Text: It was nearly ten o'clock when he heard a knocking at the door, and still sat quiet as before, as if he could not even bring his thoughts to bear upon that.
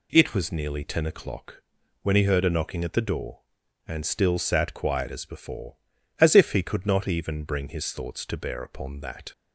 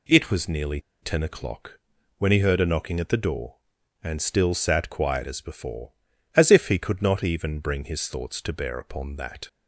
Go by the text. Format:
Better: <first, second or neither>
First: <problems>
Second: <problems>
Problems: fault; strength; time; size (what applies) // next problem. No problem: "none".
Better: first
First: pauses between "o'clock" and "when"; at 1.6 s; 0.39 s long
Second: pauses between "nearly" and "ten"; slight; at 0.7 s; 0.22 s long // pauses between "o'clock" and "when"; at 1.7 s; 0.38 s long